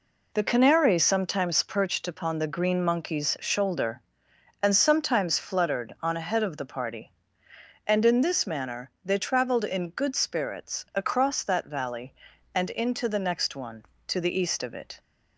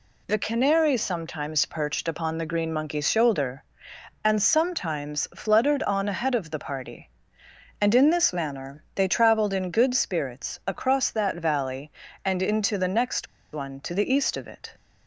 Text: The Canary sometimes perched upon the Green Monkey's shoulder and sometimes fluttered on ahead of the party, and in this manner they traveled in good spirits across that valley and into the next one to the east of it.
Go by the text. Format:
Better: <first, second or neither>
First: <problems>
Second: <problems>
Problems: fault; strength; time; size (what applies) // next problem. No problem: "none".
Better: first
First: none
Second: pauses between "next" and "one"; slight; at 13.2 s; 0.26 s long